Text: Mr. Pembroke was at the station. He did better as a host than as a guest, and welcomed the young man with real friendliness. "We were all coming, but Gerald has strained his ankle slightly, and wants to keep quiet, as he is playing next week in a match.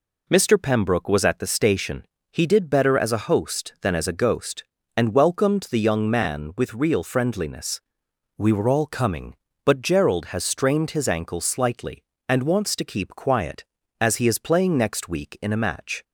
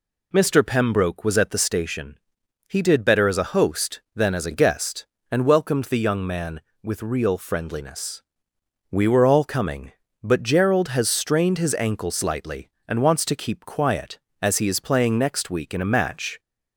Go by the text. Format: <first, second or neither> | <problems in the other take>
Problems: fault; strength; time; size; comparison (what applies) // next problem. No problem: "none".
second | says "ghost" for "guest"; at 4.1 s